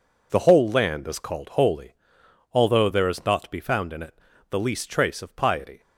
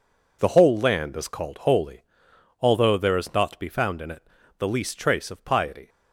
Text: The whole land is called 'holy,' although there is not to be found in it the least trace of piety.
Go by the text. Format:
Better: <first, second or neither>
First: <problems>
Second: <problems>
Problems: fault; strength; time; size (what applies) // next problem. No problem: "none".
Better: neither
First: pauses between "it" and "the"; slight; at 4.1 s; 0.34 s long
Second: pauses between "it" and "the"; slight; at 4.2 s; 0.34 s long